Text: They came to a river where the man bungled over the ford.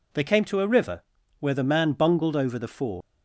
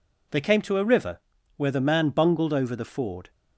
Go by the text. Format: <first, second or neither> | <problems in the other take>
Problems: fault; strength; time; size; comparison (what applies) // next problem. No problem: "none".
second | pauses between "river" and "where"; slight; at 1.0 s; 0.36 s long; slight in the second // leaves "ford" unfinished; at 3.0 s; 125 ms